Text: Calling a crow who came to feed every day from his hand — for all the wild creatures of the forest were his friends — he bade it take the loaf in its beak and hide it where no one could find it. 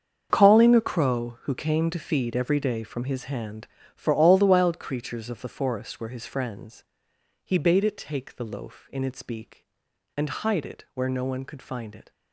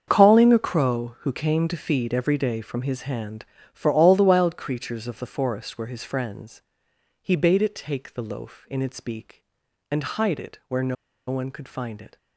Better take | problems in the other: first | starts louder than the rest; until 1.0 s; 7 dB; also in the first // pauses between "no" and "one"; slight; at 10.9 s; 0.33 s long

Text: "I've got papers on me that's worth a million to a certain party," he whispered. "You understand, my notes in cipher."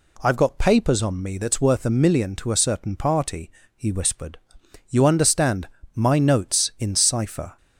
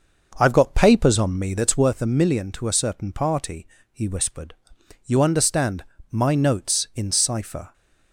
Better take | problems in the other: first | starts louder than the rest; noticeable; until 1.9 s; 6 dB

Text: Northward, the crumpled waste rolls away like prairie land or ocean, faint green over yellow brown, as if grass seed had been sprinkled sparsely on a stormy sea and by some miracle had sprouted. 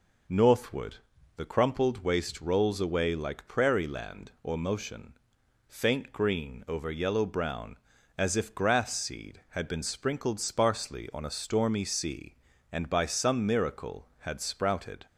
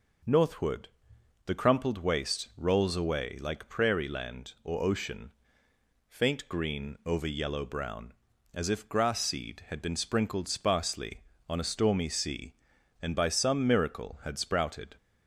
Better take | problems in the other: second | says "motion" for "ocean"; at 4.5 s

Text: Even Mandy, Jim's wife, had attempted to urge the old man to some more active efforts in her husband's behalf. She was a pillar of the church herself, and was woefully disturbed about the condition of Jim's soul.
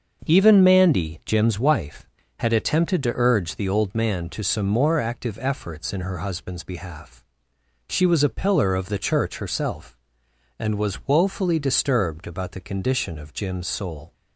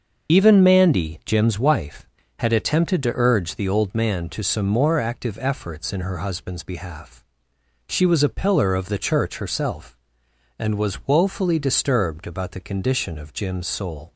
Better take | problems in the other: first | loses the start of "Even"; at 0.2 s; 85 ms // starts louder than the rest; until 1.3 s; 6.5 dB; also in the first

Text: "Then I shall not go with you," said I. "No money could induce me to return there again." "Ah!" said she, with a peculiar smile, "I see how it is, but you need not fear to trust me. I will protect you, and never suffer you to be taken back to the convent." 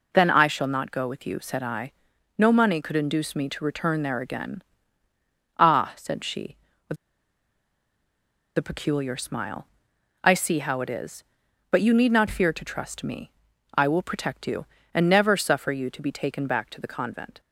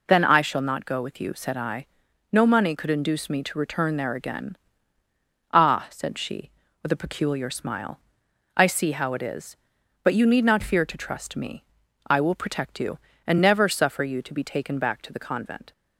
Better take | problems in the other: second | pauses between "with" and "a"; strong; at 6.9 s; 1.6 s long

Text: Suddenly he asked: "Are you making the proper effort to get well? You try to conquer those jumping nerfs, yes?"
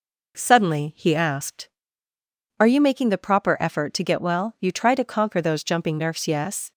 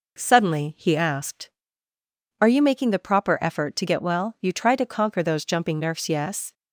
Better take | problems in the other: neither | none

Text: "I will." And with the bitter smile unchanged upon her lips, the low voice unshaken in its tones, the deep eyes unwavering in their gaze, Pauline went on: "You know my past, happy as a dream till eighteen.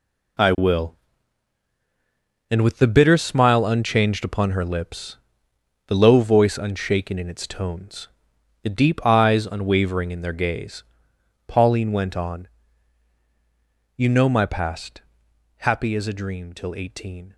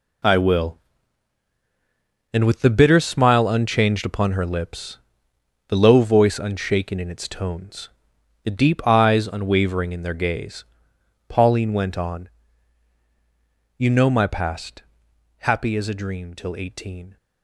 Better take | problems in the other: neither | none

